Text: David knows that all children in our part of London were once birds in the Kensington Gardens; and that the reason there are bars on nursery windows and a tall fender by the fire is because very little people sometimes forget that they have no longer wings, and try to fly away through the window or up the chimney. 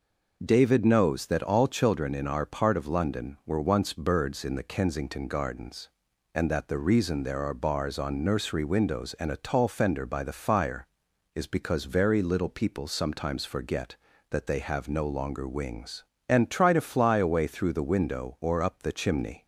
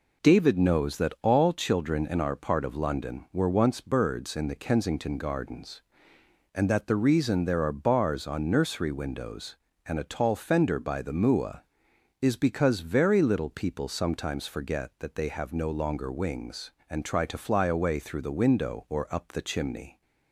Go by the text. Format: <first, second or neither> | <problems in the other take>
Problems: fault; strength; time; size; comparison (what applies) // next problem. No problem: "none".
first | says "mua" for "fire"; at 11.1 s